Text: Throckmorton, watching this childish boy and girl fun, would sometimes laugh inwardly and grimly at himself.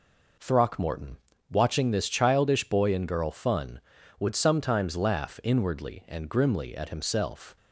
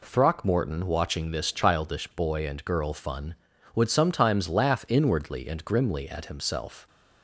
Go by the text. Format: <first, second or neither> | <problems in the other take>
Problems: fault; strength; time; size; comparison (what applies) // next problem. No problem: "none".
neither | none